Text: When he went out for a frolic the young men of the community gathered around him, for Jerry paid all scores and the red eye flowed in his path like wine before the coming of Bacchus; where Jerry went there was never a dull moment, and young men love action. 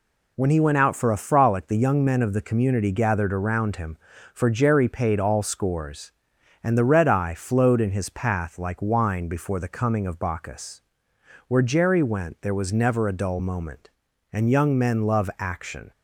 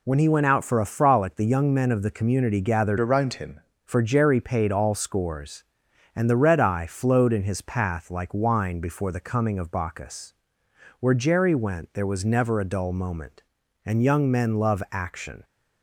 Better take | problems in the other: first | changes voice from "around" to "him"; from 2.9 to 3.5 s; 0.6 s long

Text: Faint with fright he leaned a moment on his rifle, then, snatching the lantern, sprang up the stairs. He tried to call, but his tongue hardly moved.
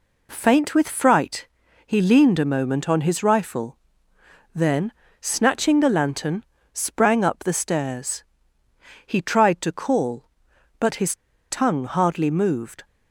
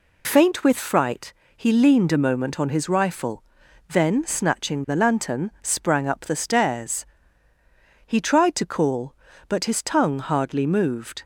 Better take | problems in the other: second | pauses between "fright" and "he"; at 1.4 s; 0.40 s long; slight in the second // pauses between "his" and "tongue"; slight; at 11.1 s; 0.33 s long

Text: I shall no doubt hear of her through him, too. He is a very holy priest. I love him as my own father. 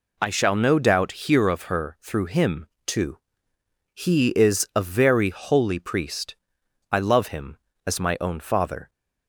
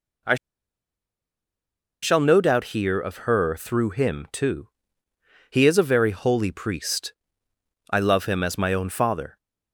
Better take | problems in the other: first | pauses between "I" and "shall"; strong; at 0.3 s; 1.6 s long

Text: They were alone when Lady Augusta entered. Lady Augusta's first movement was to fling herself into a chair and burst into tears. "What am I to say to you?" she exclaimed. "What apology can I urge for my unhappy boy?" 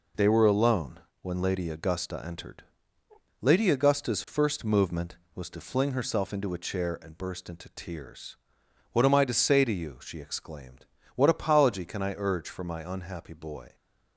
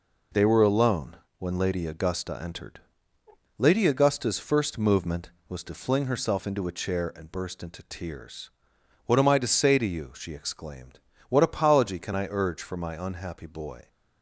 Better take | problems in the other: neither | pauses between "alone" and "when"; slight; the same in both

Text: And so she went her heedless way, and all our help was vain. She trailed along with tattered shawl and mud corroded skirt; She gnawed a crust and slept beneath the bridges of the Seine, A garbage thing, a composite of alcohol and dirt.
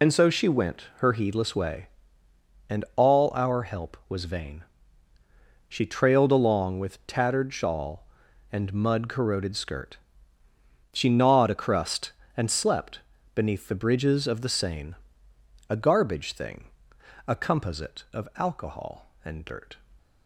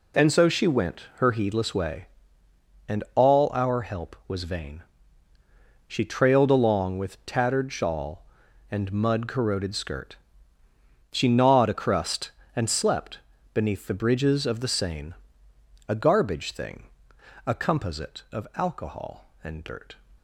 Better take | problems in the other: second | loses the start of "And"; at 0.0 s; 60 ms // pauses between "slept" and "beneath"; slight; at 13.0 s; 0.34 s long; slight in the second

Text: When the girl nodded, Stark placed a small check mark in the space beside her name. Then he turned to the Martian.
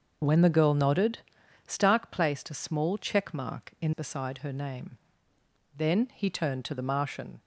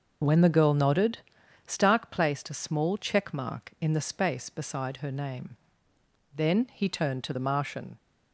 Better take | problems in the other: second | starts louder than the rest; until 1.7 s; 6.5 dB // skips "the space"; at 3.9 s

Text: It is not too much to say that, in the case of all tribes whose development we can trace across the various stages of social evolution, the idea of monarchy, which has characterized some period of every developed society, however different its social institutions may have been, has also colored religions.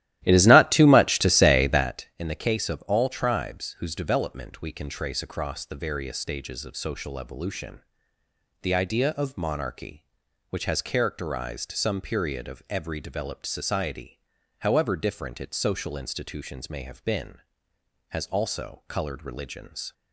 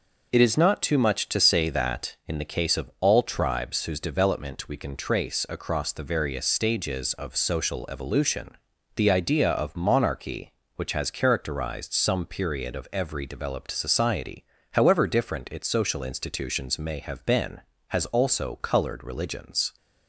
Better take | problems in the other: second | starts louder than the rest; strong; until 2.0 s; 14 dB

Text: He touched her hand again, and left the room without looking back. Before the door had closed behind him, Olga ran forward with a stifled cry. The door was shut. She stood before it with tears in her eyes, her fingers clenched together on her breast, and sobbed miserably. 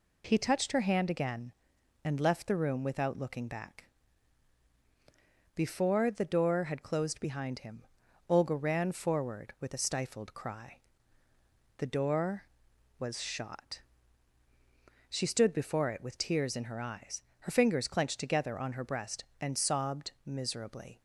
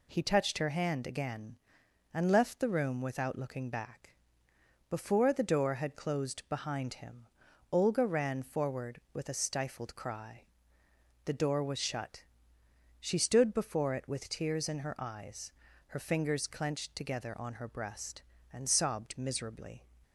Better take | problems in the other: second | says "shot" for "shut"; at 13.2 s // pauses between "sobbed" and "miserably"; slight; at 20.0 s; 0.16 s long

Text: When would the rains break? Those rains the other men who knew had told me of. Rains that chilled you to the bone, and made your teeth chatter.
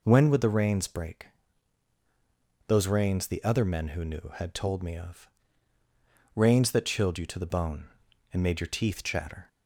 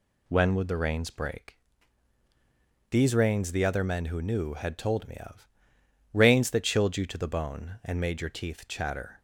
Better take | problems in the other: first | says "These" for "Those"; at 2.9 s

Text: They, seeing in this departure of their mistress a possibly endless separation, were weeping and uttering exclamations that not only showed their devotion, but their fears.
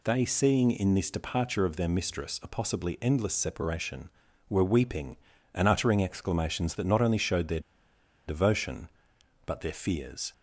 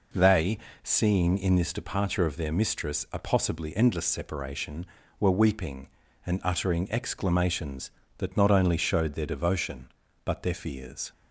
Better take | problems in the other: second | pauses between "their" and "devotion"; noticeable; at 7.5 s; 0.67 s long

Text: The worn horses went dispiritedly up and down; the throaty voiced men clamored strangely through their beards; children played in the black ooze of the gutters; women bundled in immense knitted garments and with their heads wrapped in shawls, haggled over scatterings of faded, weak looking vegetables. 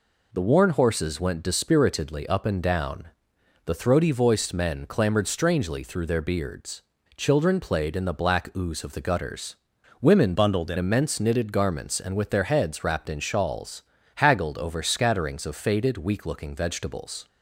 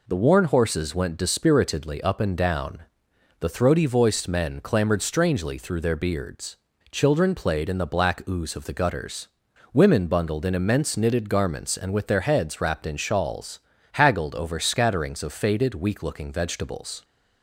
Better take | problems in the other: second | changes voice from "bundled" to "in"; from 10.3 to 10.7 s; 0.4 s long

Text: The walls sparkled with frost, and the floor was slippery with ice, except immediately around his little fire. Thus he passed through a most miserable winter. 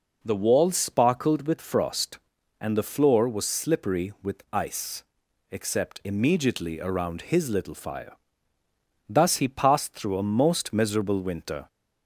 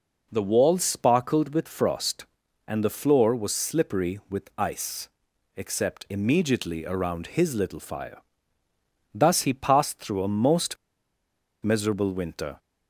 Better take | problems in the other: first | pauses between "most" and "miserable"; noticeable; at 10.7 s; 0.86 s long

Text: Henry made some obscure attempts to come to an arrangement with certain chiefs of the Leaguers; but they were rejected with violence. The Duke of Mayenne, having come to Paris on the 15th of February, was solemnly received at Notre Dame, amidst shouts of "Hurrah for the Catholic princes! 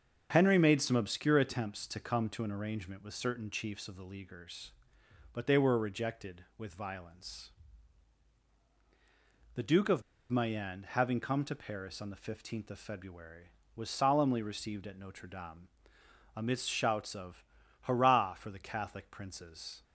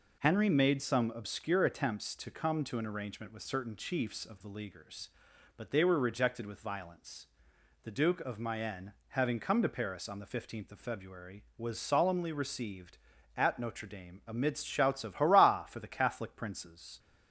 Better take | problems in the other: second | starts louder than the rest; until 1.3 s; 6.5 dB // pauses between "of" and "Mayenne"; slight; at 10.0 s; 0.30 s long // pauses between "of" and "Hurrah"; at 17.4 s; 0.38 s long

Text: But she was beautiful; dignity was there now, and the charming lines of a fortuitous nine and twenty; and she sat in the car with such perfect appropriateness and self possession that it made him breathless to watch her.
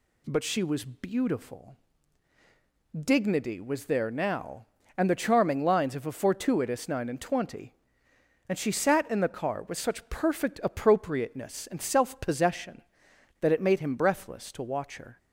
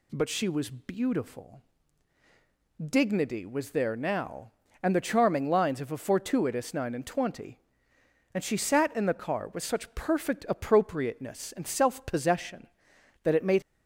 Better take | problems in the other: first | stops before "him breathless to watch her"; at 13.6 s

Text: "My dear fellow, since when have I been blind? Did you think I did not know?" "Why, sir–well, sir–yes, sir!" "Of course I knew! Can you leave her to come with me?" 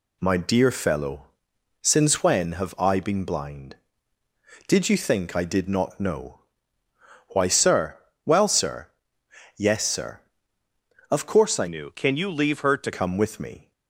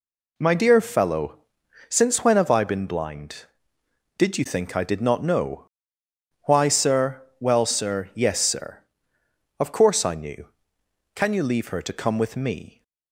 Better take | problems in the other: second | changes voice from "knew" to "to"; from 11.6 to 12.9 s; 1.3 s long

